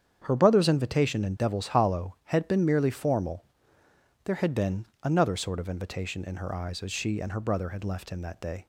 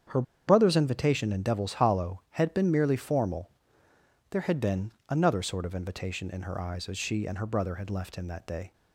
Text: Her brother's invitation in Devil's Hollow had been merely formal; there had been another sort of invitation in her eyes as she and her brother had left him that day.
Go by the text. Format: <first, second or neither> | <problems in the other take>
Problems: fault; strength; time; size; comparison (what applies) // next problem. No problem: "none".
first | starts louder than the rest; strong; until 1.3 s; 8.5 dB; strong in the first // pauses between "Her" and "brother's"; slight; at 0.2 s; 0.25 s long // pauses between "been" and "another"; slight; at 4.9 s; 0.16 s long; slight in the first